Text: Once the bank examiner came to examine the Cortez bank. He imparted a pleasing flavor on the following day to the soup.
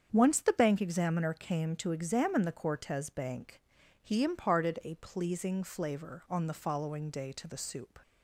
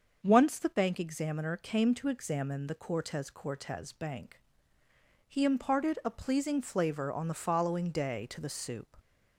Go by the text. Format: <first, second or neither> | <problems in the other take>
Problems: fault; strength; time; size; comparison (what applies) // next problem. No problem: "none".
first | starts louder than the rest; until 1.2 s; 6.5 dB; strong in the first // says "Cortez" twice; at 3.3 s